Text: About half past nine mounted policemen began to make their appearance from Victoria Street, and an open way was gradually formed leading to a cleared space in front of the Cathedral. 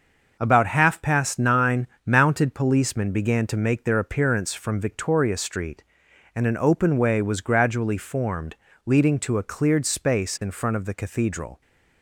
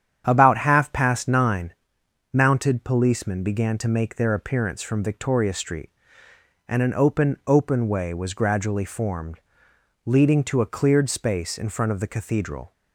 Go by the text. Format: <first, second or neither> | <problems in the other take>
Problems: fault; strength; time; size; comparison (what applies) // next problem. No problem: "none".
first | starts louder than the rest; strong; until 1.2 s; 9 dB // pauses between "nine" and "mounted"; noticeable; at 1.7 s; 0.62 s long; slight in the first // says "open" twice; at 7.4 s // pauses between "formed" and "leading"; noticeable; at 9.3 s; 0.66 s long; slight in the first